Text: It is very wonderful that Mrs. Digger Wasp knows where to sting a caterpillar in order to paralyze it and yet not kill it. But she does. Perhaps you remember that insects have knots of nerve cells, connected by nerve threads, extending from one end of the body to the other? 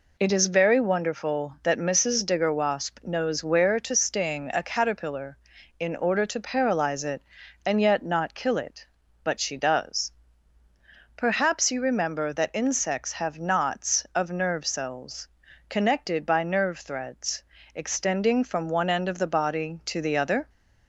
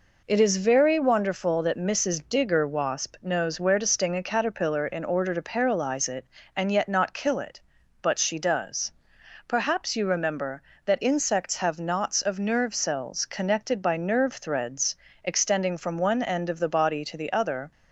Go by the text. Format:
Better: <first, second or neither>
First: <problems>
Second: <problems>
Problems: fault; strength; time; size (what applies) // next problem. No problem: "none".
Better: neither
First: none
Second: none